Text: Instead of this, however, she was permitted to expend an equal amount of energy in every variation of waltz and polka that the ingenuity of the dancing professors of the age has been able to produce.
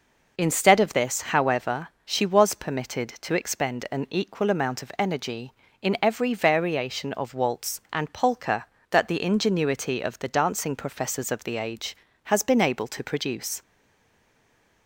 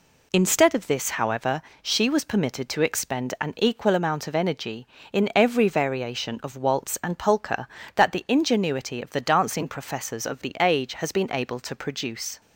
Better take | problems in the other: second | stays silent after the last word; noticeable; from 13.6 s on; 1.2 s long

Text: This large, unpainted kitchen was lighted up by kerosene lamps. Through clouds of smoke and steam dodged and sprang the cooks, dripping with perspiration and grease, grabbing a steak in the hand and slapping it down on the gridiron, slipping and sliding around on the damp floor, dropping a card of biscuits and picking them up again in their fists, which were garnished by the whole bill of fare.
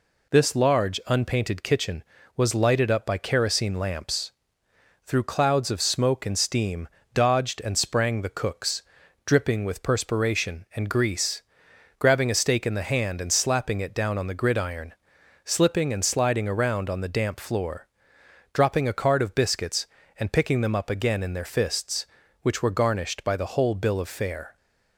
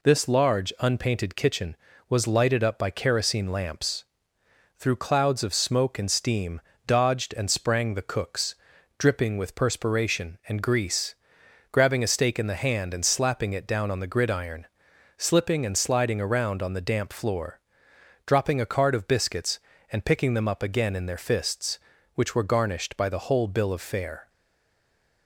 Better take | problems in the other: first | pauses between "steam" and "dodged"; slight; at 6.6 s; 0.26 s long; slight in the first // stays silent after the last word; from 24.2 s on; 1.0 s long

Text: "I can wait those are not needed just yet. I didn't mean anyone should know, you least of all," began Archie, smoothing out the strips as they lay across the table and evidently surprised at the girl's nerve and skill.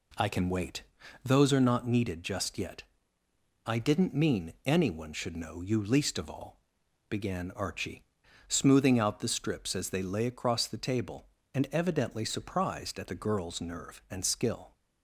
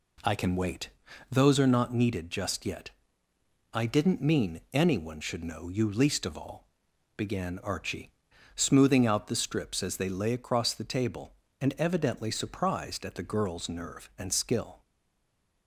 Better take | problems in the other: first | pauses between "wait" and "those"; at 0.8 s; 0.42 s long; also in the first // stays silent after the last word; slight; from 14.8 s on; 0.8 s long

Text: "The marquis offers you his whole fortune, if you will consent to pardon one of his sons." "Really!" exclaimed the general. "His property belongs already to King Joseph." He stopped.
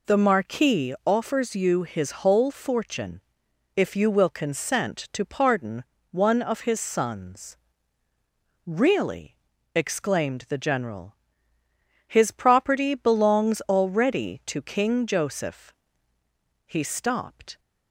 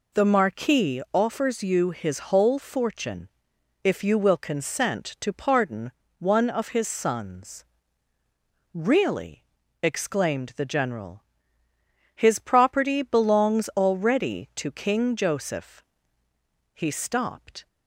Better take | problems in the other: neither | pauses between "pardon" and "one"; slight; the same in both

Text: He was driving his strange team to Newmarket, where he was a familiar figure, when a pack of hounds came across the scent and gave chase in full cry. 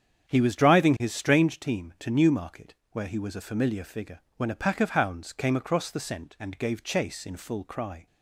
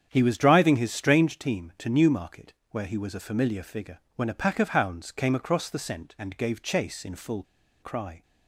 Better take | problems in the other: first | starts louder than the rest; strong; until 1.1 s; 8.5 dB; strong in the first // pauses between "full" and "cry"; at 7.4 s; 0.39 s long

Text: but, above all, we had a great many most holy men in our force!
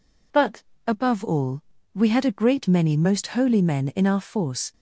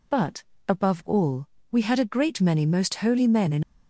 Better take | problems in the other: first | stops before "our force"; at 3.6 s

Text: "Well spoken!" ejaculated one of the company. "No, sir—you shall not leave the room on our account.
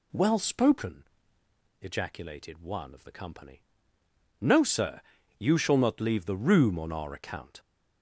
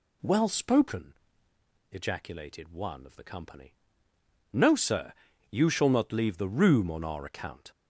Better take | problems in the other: neither | none

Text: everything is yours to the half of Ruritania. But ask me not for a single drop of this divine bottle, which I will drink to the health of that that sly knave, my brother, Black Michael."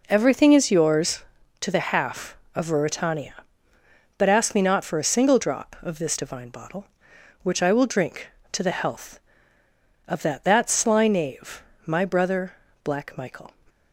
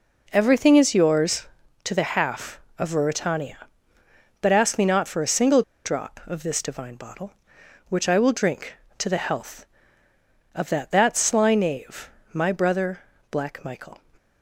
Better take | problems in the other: first | pauses between "single" and "drop"; slight; at 5.6 s; 0.23 s long

